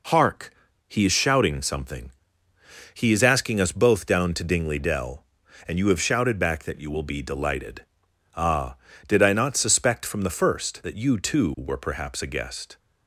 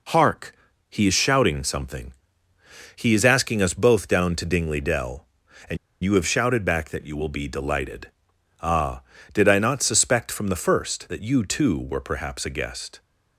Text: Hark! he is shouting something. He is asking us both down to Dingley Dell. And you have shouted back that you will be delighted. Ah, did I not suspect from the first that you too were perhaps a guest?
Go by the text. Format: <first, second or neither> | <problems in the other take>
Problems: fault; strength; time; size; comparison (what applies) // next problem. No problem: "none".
first | pauses between "And" and "you"; slight; at 5.7 s; 0.26 s long